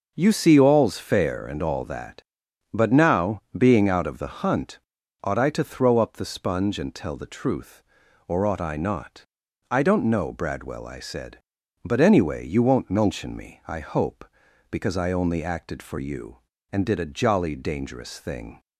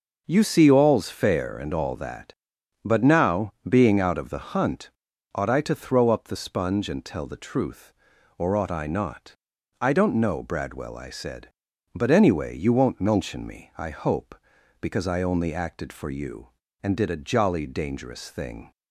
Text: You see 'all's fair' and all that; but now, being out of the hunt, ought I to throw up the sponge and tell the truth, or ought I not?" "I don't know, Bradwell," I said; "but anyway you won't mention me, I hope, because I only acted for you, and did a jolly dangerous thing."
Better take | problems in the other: neither | none

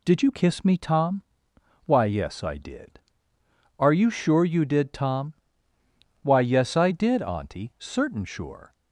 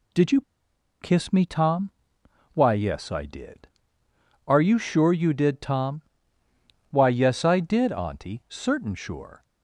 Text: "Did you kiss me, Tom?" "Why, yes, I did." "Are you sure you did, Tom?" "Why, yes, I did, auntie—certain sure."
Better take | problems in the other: first | pauses between "you" and "kiss"; noticeable; at 0.3 s; 0.61 s long

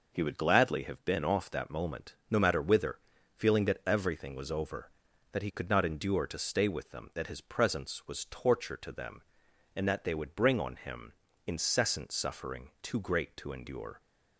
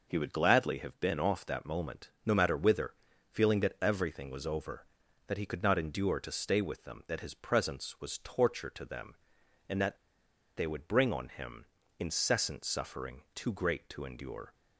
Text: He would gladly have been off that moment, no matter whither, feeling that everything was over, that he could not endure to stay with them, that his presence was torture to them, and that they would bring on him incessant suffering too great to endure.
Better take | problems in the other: first | pauses between "that" and "they"; noticeable; at 9.9 s; 0.60 s long // pauses between "him" and "incessant"; slight; at 11.6 s; 0.34 s long; slight in the first

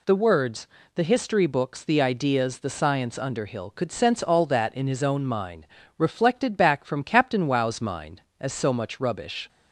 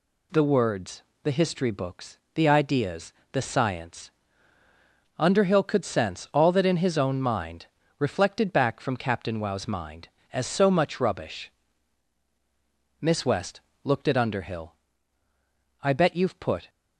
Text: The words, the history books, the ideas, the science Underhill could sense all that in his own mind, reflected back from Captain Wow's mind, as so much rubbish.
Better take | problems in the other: first | pauses between "science" and "Underhill"; at 4.1 s; 1.0 s long // goes on to say "Miss West looked at Underhill I bet you've put"; strong; from 13.0 s on; 3.6 s long

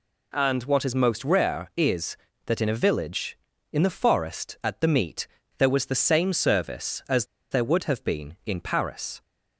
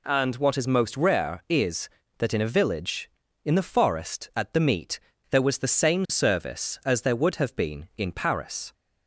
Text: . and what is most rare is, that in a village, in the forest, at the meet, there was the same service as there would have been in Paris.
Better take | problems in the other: second | pauses between "as" and "there"; slight; at 7.2 s; 0.25 s long

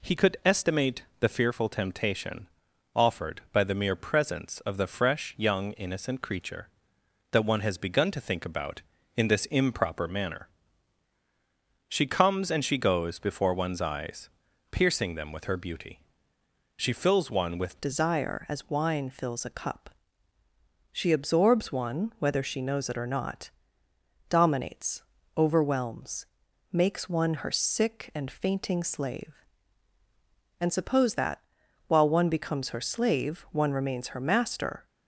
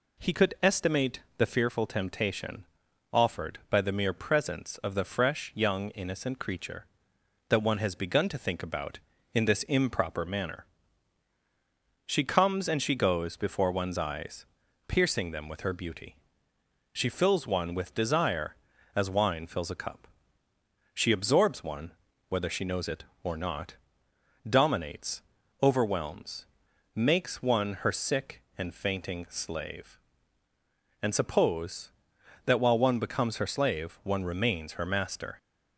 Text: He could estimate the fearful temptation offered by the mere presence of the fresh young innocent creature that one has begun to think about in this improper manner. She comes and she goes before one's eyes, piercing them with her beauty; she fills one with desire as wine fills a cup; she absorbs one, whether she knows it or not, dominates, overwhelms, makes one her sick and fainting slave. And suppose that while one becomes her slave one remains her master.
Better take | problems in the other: second | pauses between "estimate" and "the"; slight; at 1.0 s; 0.16 s long; slight in the second // pauses between "temptation" and "offered"; noticeable; at 2.4 s; 0.46 s long; noticeable in the second // changes voice at "desire"; from 17.7 s on; 17.1 s long // pauses between "that" and "while"; noticeable; at 31.4 s; 0.46 s long

